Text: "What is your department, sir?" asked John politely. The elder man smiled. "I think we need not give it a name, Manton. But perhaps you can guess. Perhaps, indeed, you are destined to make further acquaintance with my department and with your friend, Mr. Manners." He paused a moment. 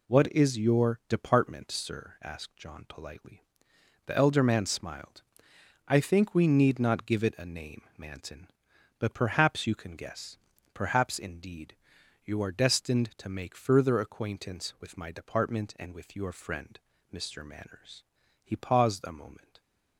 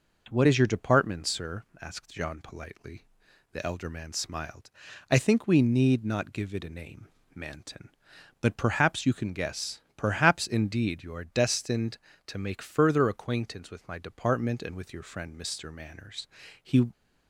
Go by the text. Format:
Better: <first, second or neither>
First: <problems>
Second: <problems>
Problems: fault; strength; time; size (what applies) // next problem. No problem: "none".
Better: first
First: none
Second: stops before "paused a moment"; at 16.9 s